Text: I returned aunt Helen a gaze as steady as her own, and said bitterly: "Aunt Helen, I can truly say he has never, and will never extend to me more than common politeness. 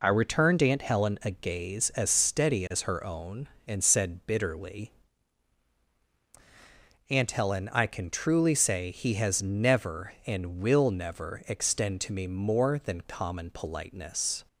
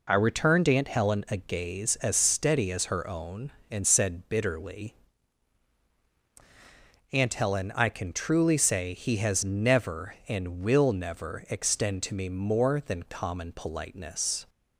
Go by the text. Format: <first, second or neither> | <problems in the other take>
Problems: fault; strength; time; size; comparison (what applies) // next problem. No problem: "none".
neither | none